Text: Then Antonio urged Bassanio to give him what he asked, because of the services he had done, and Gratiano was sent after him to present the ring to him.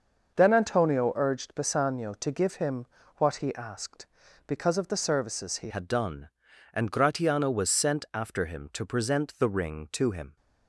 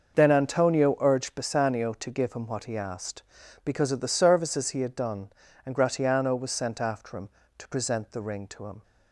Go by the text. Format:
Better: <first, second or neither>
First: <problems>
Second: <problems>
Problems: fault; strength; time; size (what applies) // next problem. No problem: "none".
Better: second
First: starts louder than the rest; noticeable; until 1.3 s; 6 dB // pauses between "him" and "what"; slight; at 2.8 s; 0.30 s long // changes voice at "had"; from 5.6 s on; 4.7 s long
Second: starts louder than the rest; until 1.1 s; 6.5 dB